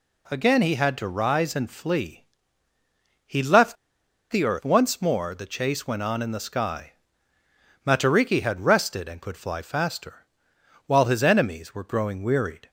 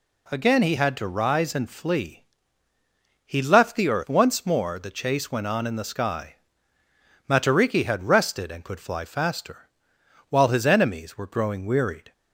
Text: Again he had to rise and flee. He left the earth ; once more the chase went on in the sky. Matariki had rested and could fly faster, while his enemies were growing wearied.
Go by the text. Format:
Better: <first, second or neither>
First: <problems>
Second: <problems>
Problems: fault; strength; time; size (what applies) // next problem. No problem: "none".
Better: second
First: pauses between "left" and "the"; noticeable; at 3.7 s; 0.55 s long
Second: none